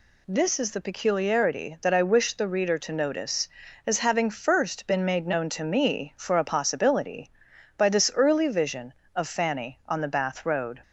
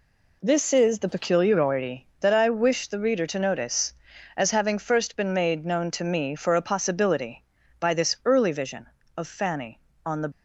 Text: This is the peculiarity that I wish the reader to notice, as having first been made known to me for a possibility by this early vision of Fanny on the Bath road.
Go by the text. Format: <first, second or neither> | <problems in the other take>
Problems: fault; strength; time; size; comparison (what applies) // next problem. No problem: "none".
first | stops before "Bath road"; at 10.3 s